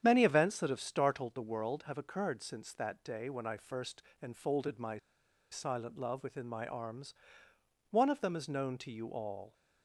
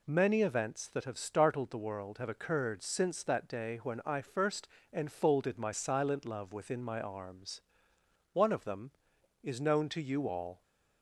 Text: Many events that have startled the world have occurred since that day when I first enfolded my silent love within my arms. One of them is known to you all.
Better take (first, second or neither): second